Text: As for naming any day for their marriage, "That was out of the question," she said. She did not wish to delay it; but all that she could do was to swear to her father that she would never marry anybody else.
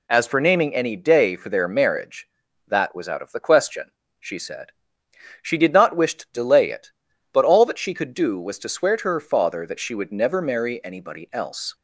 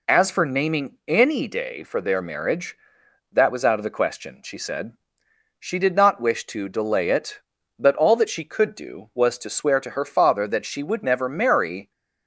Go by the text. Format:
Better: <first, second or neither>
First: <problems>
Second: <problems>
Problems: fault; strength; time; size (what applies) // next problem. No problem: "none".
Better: first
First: none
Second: stops before "anybody else"; at 11.9 s